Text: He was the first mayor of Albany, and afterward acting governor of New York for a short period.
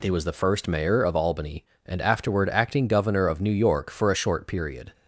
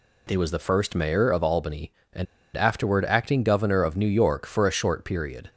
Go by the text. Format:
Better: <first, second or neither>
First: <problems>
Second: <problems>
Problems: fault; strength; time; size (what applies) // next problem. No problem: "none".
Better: first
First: none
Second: pauses between "and" and "afterward"; slight; at 2.2 s; 0.30 s long